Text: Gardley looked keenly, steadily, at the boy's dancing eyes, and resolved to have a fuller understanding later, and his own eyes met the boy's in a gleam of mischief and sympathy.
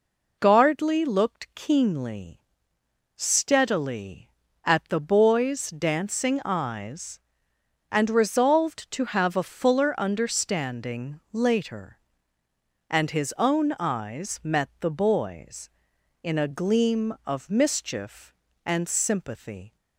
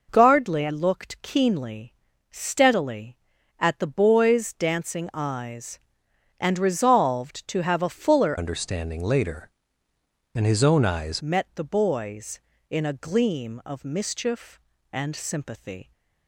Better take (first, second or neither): first